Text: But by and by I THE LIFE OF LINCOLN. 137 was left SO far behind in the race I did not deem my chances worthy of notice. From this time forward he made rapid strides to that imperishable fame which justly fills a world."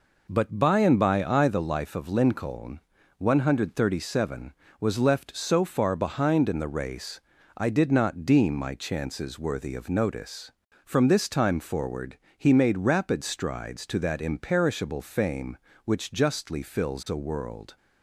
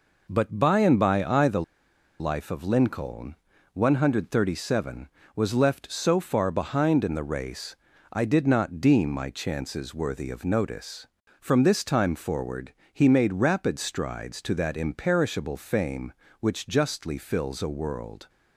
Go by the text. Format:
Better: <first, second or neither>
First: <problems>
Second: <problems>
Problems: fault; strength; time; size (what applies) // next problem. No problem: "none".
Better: first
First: pauses between "race" and "I"; slight; at 7.1 s; 0.36 s long // pauses between "forward" and "he"; slight; at 12.1 s; 0.20 s long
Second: pauses between "THE" and "LIFE"; noticeable; at 1.6 s; 0.58 s long // pauses between "race" and "I"; slight; at 7.7 s; 0.36 s long // pauses between "forward" and "he"; slight; at 12.7 s; 0.20 s long